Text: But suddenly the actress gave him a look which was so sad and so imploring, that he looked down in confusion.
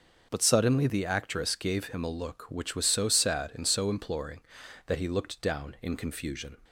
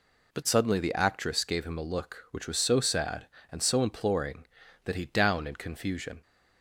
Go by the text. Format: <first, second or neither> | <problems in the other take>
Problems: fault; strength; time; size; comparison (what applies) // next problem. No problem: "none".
first | skips "looked"; at 5.0 s